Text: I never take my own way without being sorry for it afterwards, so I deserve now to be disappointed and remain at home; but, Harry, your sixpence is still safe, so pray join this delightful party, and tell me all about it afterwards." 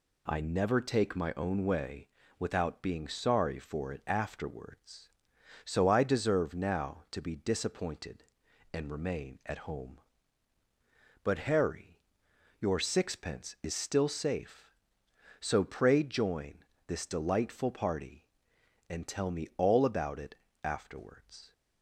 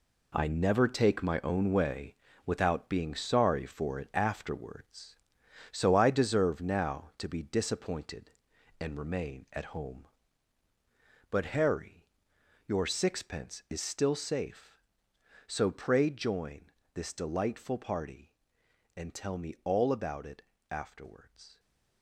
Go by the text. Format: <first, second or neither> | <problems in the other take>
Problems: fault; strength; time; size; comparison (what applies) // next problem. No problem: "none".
first | gets quieter; strong; throughout; 9.5 dB // pauses between "way" and "without"; slight; at 2.1 s; 0.30 s long; slight in the first // pauses between "join" and "this"; slight; at 16.7 s; 0.24 s long; slight in the first // pauses between "it" and "afterwards"; slight; at 20.4 s; 0.30 s long; slight in the first